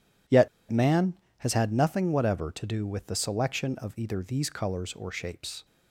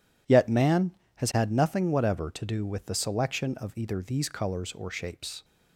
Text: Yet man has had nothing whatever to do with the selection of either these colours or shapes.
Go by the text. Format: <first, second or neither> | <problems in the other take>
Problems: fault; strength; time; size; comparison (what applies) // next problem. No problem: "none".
second | pauses between "Yet" and "man"; slight; at 0.4 s; 0.22 s long